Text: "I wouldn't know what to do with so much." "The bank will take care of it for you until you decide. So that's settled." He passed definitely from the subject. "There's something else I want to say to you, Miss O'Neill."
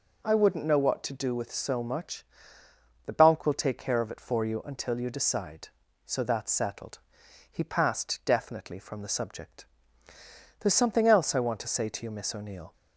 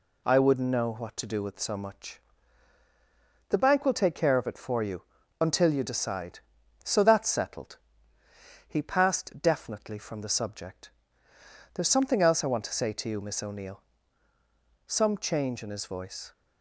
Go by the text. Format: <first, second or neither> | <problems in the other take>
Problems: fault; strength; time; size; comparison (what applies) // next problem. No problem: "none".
first | pauses between "you" and "until"; slight; at 5.0 s; 0.36 s long // goes on to say "Some change in his voice"; from 14.8 s on; 1.4 s long